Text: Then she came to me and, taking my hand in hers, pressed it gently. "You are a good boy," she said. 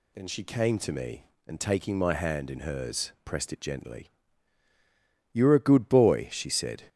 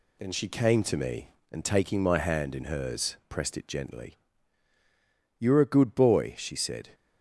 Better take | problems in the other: first | gets quieter; slight; throughout; 2.5 dB

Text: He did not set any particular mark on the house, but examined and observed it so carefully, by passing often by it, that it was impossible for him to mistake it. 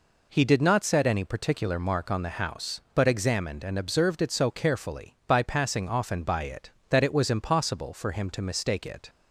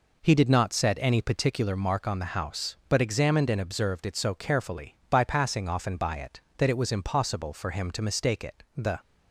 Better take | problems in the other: first | goes on to say "The"; slight; from 8.7 s on; 0.24 s long

